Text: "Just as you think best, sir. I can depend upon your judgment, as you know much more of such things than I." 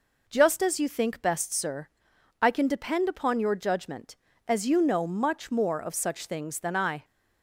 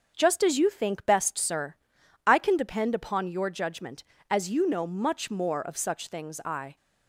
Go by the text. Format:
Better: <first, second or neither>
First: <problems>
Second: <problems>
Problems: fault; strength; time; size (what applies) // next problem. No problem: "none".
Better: first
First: none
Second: starts louder than the rest; until 1.1 s; 7 dB // skips "than"; at 6.4 s